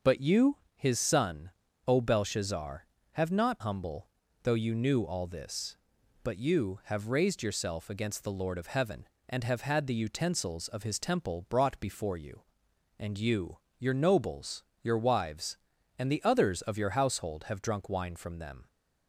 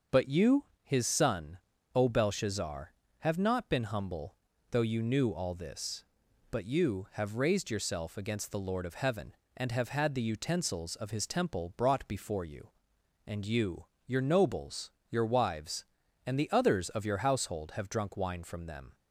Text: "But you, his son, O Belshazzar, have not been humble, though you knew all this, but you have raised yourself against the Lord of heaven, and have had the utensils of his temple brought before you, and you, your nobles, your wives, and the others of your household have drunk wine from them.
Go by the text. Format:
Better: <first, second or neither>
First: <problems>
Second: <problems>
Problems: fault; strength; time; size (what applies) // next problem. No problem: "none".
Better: second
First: starts louder than the rest; until 1.2 s; 6.5 dB // skips "been"; at 3.6 s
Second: starts louder than the rest; until 1.3 s; 6.5 dB